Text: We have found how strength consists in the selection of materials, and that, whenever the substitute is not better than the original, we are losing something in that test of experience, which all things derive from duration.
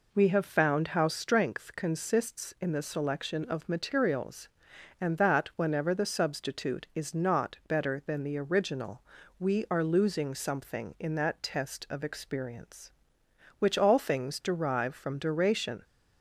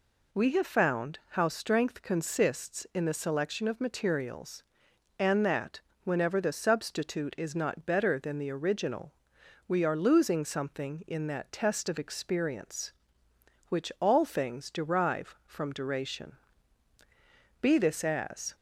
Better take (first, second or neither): first